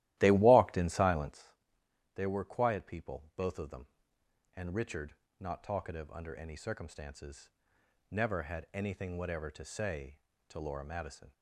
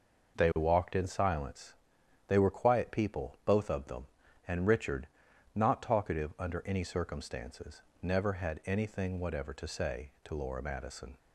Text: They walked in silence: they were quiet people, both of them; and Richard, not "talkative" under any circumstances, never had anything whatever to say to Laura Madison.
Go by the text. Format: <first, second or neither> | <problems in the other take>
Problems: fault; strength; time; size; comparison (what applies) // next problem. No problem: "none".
second | starts louder than the rest; strong; until 1.4 s; 15 dB